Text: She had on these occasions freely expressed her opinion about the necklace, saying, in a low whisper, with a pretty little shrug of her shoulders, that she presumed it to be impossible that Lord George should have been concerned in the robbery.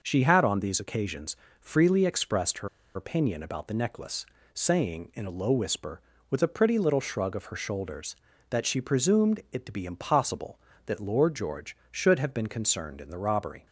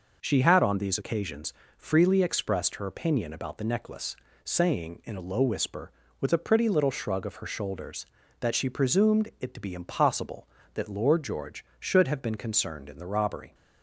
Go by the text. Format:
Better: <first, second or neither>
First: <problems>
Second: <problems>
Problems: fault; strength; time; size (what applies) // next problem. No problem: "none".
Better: second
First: pauses between "occasions" and "freely"; slight; at 1.3 s; 0.24 s long // pauses between "her" and "opinion"; slight; at 2.6 s; 0.27 s long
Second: pauses between "occasions" and "freely"; slight; at 1.5 s; 0.24 s long